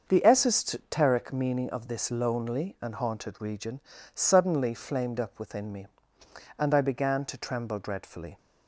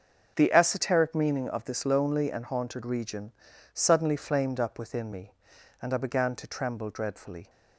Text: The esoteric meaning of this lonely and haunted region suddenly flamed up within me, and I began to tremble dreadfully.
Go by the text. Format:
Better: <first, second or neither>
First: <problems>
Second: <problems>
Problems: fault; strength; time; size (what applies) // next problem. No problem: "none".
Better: neither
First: starts louder than the rest; until 1.0 s; 6 dB // pauses between "region" and "suddenly"; slight; at 3.8 s; 0.32 s long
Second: starts louder than the rest; until 1.3 s; 6.5 dB // pauses between "region" and "suddenly"; at 3.3 s; 0.40 s long